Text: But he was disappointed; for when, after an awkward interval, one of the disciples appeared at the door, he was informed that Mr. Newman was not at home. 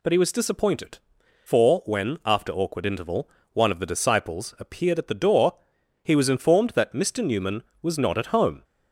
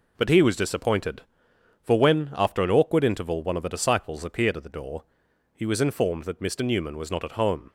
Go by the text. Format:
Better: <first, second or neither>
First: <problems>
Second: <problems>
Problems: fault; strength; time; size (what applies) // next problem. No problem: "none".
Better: second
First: skips "an"; at 2.5 s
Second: none